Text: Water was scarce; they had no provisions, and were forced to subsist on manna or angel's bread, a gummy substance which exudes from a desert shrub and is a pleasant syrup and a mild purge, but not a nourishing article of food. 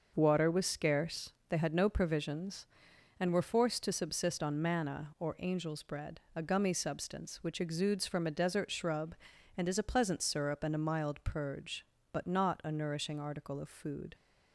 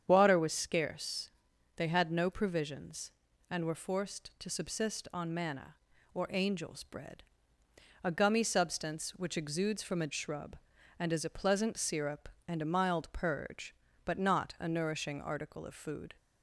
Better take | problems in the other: first | starts louder than the rest; strong; until 1.0 s; 8 dB; noticeable in the first // skips "desert"; at 10.1 s

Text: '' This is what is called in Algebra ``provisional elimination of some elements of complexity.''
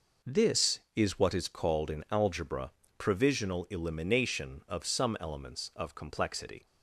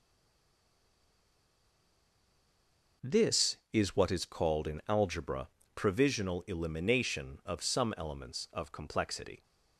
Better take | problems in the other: first | stays silent before the first word; strong; until 3.0 s; 3.0 s long // pauses between "Algebra" and "provisional"; slight; at 5.4 s; 0.26 s long; slight in the first

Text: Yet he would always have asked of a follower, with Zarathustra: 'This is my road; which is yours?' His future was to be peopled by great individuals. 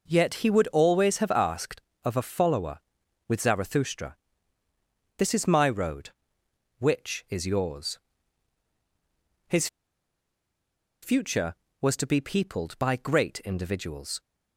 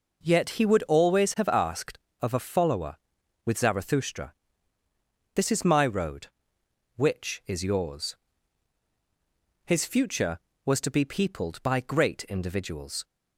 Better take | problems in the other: second | pauses between "His" and "future"; strong; at 9.6 s; 1.3 s long

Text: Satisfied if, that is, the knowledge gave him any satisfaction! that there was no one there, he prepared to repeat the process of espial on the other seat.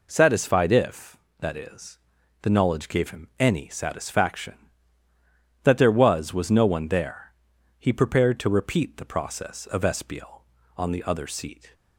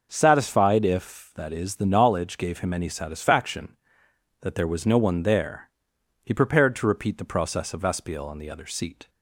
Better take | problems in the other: second | says "was" twice; at 6.3 s

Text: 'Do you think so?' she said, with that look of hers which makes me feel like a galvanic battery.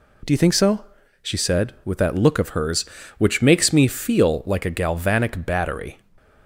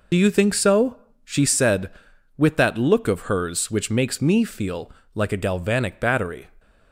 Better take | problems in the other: first | loses the start of "Do"; at 0.1 s; 45 ms // pauses between "feel" and "like"; slight; at 4.9 s; 0.22 s long

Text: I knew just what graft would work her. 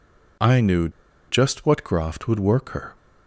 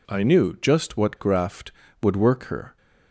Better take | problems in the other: second | pauses between "knew" and "just"; at 0.8 s; 0.39 s long

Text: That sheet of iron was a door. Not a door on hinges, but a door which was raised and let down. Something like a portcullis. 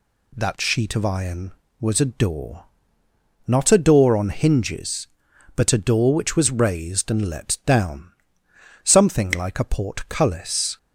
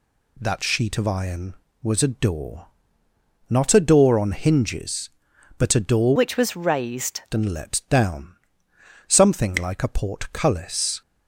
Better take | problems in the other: first | changes voice from "which" to "raised"; from 6.1 to 7.2 s; 1.1 s long

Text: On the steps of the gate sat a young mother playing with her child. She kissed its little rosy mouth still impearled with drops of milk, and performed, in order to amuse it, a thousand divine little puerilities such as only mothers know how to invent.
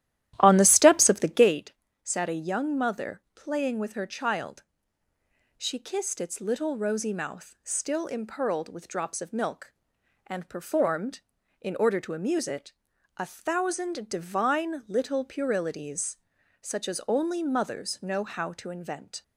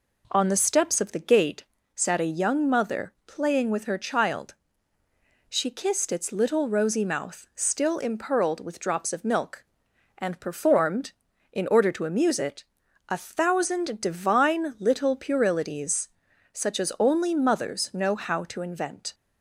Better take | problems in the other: second | starts louder than the rest; strong; until 1.6 s; 13.5 dB // pauses between "gate" and "sat"; slight; at 1.7 s; 0.30 s long; slight in the second // pauses between "puerilities" and "such"; at 16.1 s; 0.44 s long; also in the second

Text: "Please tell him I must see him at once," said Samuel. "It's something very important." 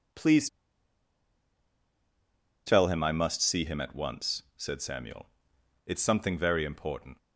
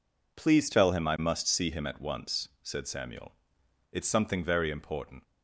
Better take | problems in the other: second | pauses between "Please" and "tell"; strong; at 0.4 s; 2.1 s long

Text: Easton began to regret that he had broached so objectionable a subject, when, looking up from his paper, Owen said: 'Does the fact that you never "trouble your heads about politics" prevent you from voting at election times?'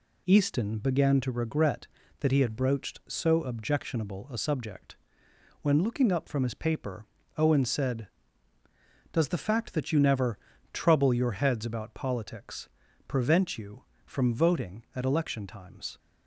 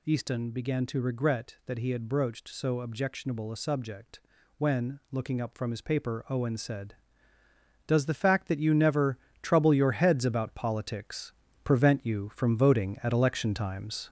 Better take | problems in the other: first | gets louder; noticeable; throughout; 5.5 dB // pauses between "never" and "trouble"; slight; at 9.1 s; 0.24 s long; slight in the first // pauses between "politics" and "prevent"; slight; at 11.3 s; 0.32 s long; also in the first

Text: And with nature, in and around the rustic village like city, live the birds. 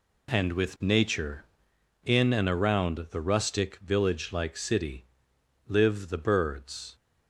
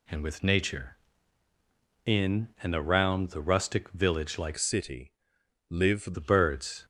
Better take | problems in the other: first | changes voice from "city" to "live"; from 4.5 to 6.1 s; 1.6 s long

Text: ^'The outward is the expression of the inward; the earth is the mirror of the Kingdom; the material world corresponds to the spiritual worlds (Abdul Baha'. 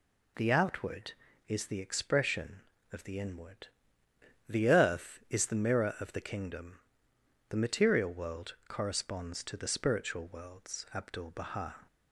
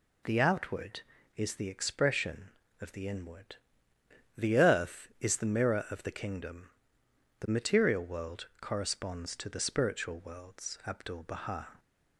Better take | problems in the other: neither | none

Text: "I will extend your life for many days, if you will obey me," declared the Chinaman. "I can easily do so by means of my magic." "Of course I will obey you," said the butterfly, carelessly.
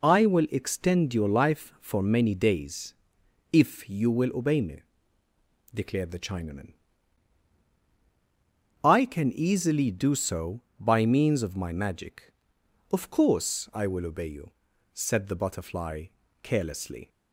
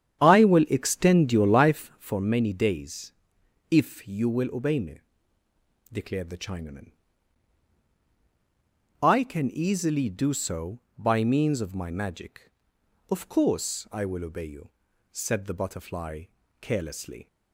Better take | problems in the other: first | starts louder than the rest; strong; until 2.1 s; 9 dB

